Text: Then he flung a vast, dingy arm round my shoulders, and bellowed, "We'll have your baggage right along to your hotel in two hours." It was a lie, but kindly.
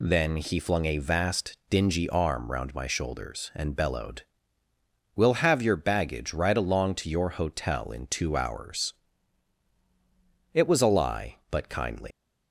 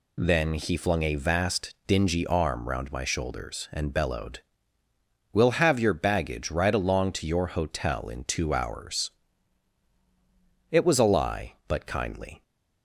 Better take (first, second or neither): second